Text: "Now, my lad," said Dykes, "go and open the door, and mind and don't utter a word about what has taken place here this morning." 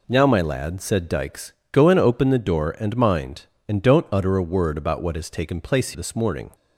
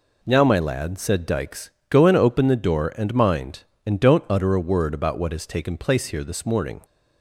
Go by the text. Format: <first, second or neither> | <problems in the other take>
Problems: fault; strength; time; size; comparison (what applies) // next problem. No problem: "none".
second | skips "here"; at 5.9 s